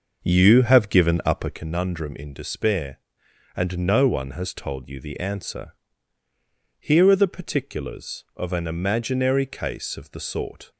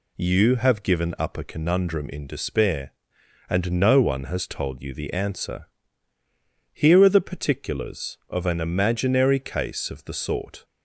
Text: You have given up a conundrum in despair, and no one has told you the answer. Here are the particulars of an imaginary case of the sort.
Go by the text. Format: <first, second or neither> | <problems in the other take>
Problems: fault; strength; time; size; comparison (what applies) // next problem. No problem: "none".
second | starts louder than the rest; noticeable; until 1.7 s; 6 dB